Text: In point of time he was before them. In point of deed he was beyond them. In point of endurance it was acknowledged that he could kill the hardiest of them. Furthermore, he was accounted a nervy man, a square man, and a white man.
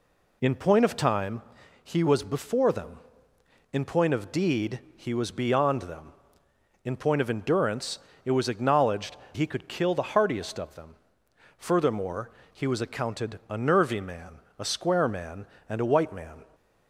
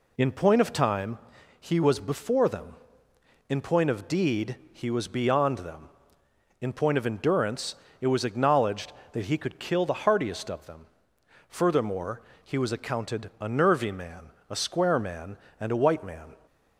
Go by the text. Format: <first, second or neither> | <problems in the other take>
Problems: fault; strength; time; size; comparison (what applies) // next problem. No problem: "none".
second | pauses between "time" and "he"; at 1.4 s; 0.42 s long; also in the second // pauses between "deed" and "he"; slight; at 4.7 s; 0.16 s long; slight in the second // pauses between "endurance" and "it"; slight; at 7.9 s; 0.26 s long; slight in the second // skips "that"; at 9.2 s